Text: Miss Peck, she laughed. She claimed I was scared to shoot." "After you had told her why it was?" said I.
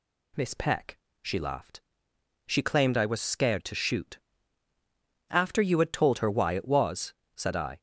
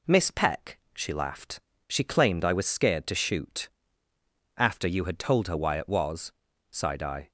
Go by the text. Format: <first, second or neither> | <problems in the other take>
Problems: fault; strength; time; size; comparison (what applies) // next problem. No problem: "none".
first | says "sighed" for "said"; at 6.7 s